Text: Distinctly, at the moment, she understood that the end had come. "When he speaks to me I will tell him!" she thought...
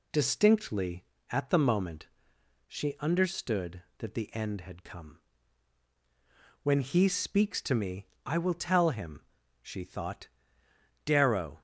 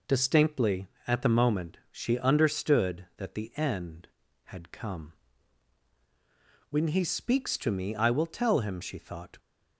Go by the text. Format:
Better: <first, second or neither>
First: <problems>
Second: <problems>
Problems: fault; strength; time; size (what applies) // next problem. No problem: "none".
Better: second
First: pauses between "me" and "I"; slight; at 8.0 s; 0.18 s long // goes on to say "Darrow"; from 11.0 s on; 0.56 s long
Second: none